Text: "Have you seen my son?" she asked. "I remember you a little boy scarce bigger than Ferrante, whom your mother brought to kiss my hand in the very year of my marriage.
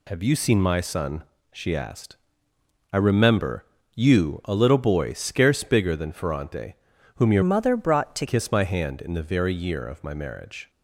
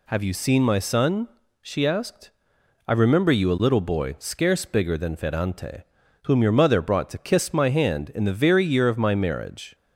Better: second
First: pauses between "remember" and "you"; slight; at 3.6 s; 0.28 s long // changes voice from "mother" to "to"; from 7.4 to 8.2 s; 0.8 s long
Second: none

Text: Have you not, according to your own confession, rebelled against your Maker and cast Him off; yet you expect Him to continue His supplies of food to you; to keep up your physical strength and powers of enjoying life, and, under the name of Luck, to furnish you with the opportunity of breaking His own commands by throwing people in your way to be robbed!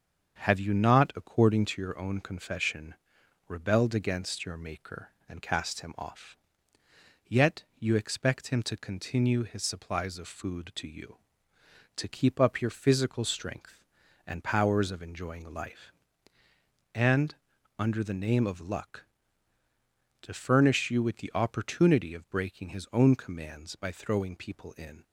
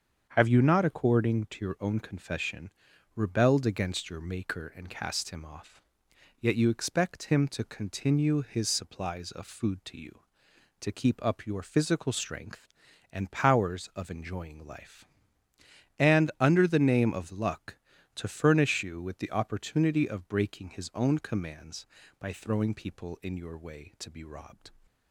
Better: second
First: starts louder than the rest; strong; until 1.4 s; 7.5 dB // pauses between "yet" and "you"; slight; at 7.6 s; 0.16 s long // stops before "your way to be robbed"; at 25.0 s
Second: starts louder than the rest; strong; until 1.3 s; 7 dB

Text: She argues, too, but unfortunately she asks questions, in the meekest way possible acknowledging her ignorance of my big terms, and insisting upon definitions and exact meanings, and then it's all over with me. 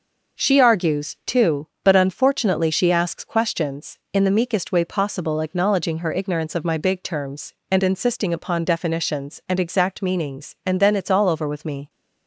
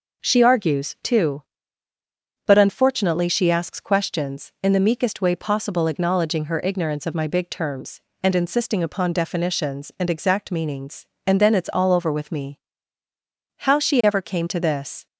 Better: first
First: none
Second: goes on to say "How she ever came to this"; from 13.5 s on; 1.4 s long

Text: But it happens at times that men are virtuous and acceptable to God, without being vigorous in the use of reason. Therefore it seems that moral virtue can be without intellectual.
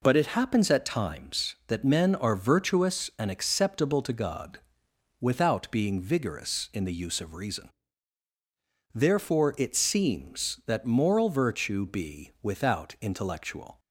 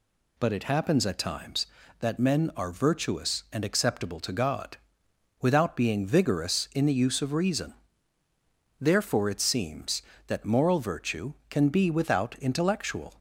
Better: second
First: skips "can"; at 11.8 s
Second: none

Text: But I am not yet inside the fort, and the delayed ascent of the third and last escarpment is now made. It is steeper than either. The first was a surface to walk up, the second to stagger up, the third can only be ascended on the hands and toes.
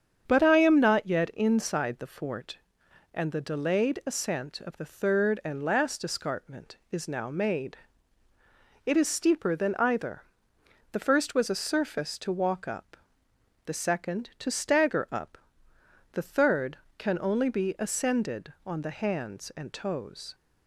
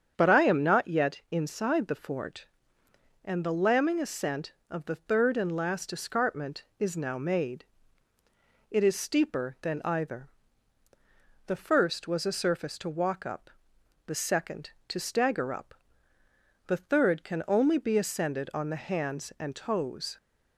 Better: first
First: starts louder than the rest; strong; until 1.2 s; 8 dB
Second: starts louder than the rest; strong; until 1.1 s; 8 dB // says "lambing" for "delayed"; at 3.5 s

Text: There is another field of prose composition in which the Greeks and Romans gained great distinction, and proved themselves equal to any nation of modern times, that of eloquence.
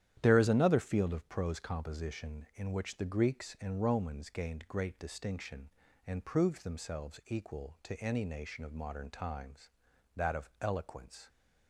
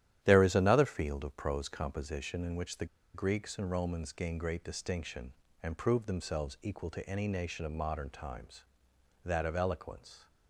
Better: first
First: starts louder than the rest; strong; until 1.2 s; 11 dB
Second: starts louder than the rest; strong; until 1.2 s; 11.5 dB // pauses between "the" and "Greeks"; slight; at 2.8 s; 0.28 s long

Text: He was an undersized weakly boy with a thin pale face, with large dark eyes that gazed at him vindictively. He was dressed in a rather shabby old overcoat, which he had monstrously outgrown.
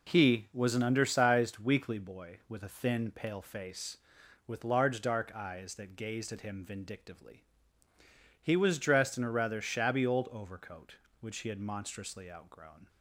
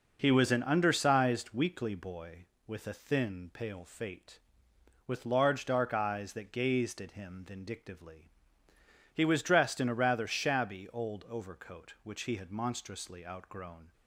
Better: first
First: none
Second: says "fate" for "face"; at 3.8 s

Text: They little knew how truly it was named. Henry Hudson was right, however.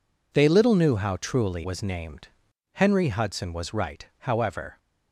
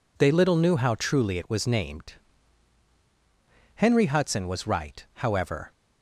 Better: second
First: skips "it"; at 1.6 s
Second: none

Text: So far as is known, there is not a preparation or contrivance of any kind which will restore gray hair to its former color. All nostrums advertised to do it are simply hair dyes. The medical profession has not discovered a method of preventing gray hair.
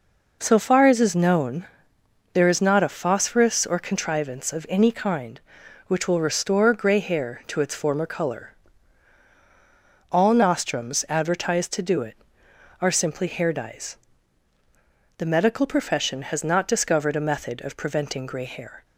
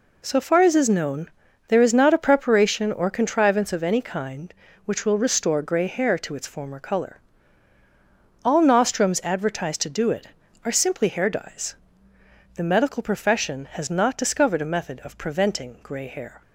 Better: second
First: says "phosphorus" for "preparation"; at 2.8 s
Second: none

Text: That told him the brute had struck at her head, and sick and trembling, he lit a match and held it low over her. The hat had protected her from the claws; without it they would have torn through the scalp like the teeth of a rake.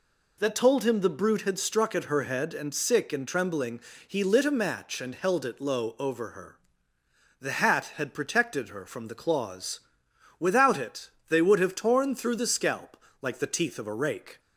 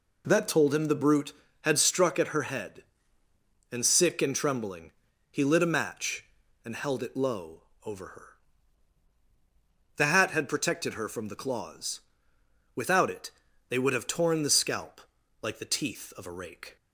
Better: first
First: pauses between "it" and "they"; slight; at 11.0 s; 0.18 s long // pauses between "scalp" and "like"; slight; at 12.9 s; 0.26 s long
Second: pauses between "low" and "over"; slight; at 7.6 s; 0.24 s long // pauses between "it" and "they"; at 13.2 s; 0.38 s long // skips "through"; at 14.4 s // pauses between "scalp" and "like"; at 14.9 s; 0.42 s long

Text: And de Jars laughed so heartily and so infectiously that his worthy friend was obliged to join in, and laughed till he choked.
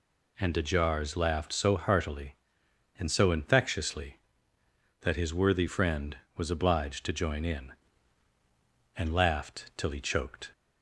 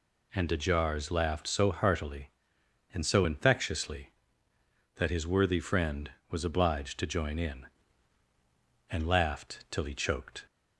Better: neither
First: none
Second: none

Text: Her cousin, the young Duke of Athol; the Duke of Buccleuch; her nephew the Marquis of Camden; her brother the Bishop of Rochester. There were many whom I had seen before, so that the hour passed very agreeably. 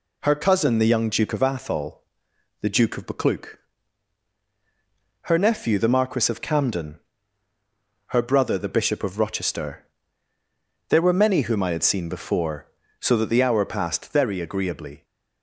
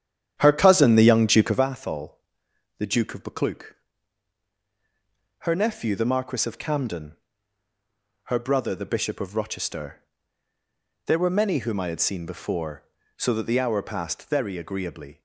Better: first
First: none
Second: starts louder than the rest; strong; until 1.7 s; 9.5 dB

